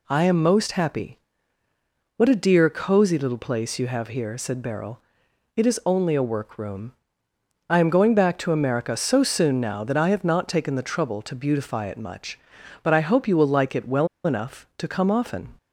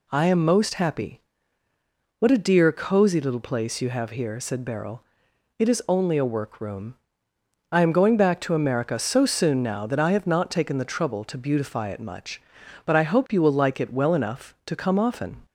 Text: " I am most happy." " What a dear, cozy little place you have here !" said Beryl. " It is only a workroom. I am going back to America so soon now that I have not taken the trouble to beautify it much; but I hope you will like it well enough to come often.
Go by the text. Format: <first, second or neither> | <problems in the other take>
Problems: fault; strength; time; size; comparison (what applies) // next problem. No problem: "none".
second | pauses between "well" and "enough"; slight; at 14.0 s; 0.17 s long